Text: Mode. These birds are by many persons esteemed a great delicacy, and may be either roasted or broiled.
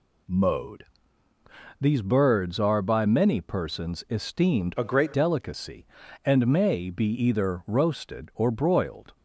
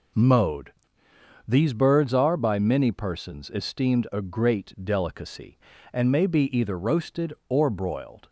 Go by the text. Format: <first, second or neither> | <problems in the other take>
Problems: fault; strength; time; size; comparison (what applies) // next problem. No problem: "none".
second | changes voice from "a" to "great"; from 4.7 to 5.1 s; 0.4 s long